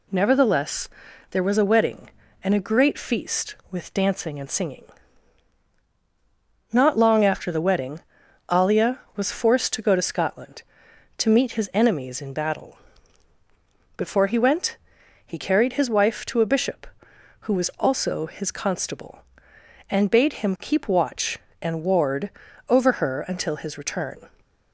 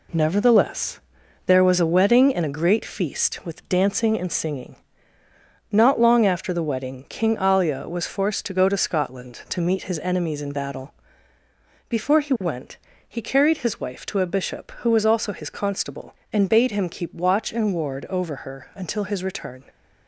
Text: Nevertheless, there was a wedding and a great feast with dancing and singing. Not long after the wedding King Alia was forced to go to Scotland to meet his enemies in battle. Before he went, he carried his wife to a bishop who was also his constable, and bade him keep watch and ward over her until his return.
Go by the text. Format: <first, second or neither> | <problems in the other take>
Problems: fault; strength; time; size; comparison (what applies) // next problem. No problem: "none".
second | skips "King"; at 8.2 s // pauses between "ward" and "over"; at 22.2 s; 0.40 s long